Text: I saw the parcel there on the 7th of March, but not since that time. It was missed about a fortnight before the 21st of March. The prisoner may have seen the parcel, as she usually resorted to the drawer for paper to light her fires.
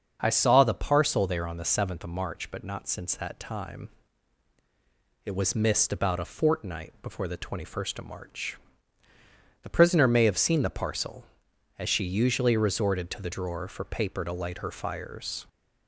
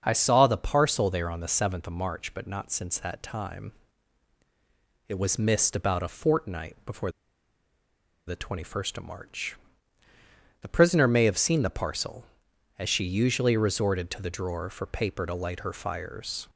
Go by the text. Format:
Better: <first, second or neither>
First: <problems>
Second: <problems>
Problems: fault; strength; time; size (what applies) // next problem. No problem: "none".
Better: first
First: starts louder than the rest; until 1.2 s; 6.5 dB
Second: starts louder than the rest; until 1.0 s; 6.5 dB // pauses between "before" and "the"; at 7.0 s; 1.1 s long